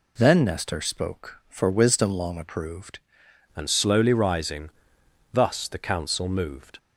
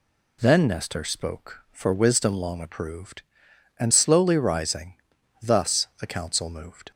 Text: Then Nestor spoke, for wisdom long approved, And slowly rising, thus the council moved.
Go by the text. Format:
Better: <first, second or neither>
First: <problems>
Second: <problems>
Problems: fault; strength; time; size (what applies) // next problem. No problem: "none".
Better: second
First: changes voice at "And"; from 3.5 s on; 3.2 s long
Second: none